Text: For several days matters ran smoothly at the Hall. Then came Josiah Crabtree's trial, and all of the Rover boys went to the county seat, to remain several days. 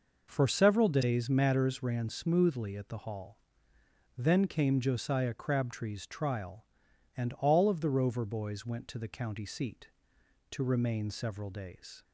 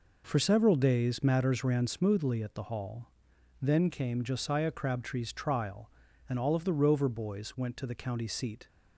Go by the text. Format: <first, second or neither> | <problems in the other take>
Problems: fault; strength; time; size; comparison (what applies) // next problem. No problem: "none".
first | stops before "to remain several days"; at 8.6 s